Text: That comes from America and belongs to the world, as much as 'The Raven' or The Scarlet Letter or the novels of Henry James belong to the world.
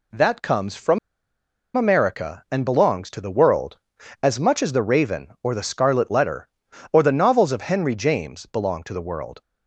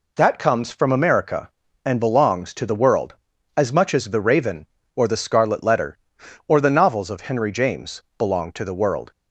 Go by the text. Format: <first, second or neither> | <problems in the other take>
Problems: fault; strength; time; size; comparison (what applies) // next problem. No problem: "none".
second | pauses between "from" and "America"; noticeable; at 0.9 s; 0.78 s long